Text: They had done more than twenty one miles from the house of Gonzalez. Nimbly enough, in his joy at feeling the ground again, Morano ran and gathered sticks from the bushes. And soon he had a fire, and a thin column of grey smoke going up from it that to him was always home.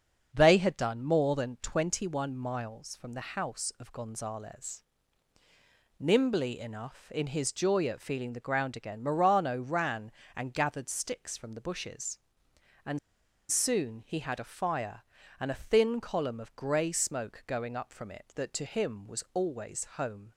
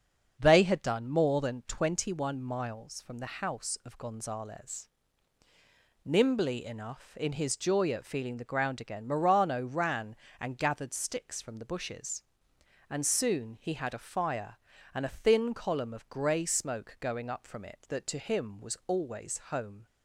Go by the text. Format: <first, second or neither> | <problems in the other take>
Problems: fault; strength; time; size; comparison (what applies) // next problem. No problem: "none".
second | starts louder than the rest; until 1.3 s; 7 dB; also in the second // pauses between "And" and "soon"; noticeable; at 12.9 s; 0.52 s long